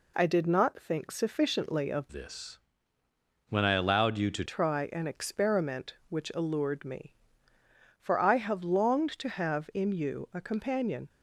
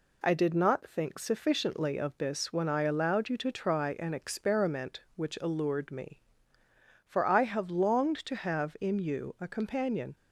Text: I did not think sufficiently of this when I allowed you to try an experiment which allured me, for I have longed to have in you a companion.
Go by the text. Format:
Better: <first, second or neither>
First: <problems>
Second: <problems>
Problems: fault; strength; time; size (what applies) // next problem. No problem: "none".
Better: second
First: changes voice from "this" to "to"; from 2.1 to 4.4 s; 2.3 s long // pauses between "this" and "when"; noticeable; at 2.5 s; 0.90 s long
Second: none